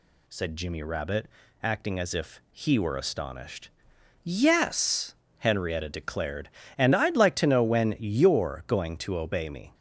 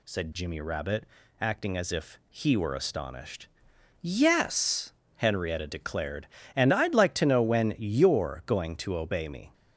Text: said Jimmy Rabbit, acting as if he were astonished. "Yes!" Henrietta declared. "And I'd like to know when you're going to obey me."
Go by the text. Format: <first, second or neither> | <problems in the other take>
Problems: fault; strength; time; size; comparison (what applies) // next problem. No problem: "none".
neither | none